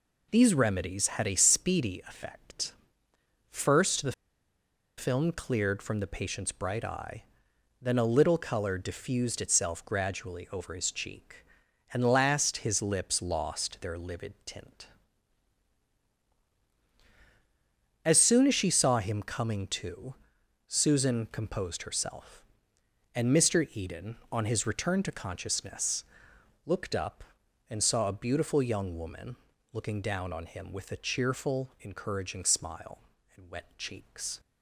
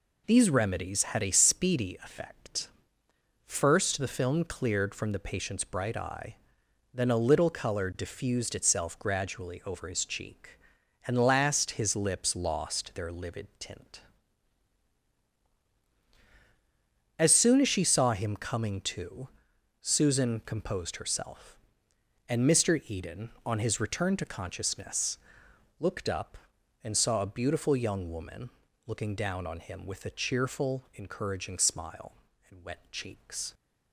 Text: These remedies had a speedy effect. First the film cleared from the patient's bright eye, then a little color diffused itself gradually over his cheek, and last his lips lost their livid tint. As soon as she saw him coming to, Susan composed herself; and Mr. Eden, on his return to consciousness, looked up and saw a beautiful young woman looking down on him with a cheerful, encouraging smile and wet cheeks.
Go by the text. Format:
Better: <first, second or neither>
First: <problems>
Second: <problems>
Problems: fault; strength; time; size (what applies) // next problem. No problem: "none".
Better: second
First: pauses between "the" and "film"; noticeable; at 4.1 s; 0.85 s long // pauses between "woman" and "looking"; slight; at 29.3 s; 0.36 s long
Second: pauses between "woman" and "looking"; slight; at 28.4 s; 0.36 s long